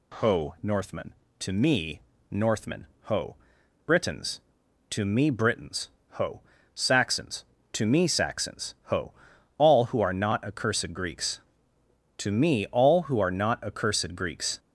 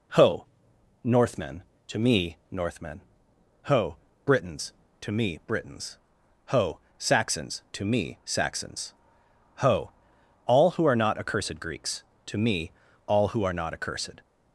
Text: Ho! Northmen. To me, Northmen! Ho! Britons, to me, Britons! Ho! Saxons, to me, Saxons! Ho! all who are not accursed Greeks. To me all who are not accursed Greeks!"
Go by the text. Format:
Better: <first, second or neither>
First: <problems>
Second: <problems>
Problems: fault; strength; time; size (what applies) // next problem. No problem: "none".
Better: first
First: none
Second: pauses between "me" and "all"; slight; at 12.7 s; 0.34 s long // stops before "Greeks"; at 14.2 s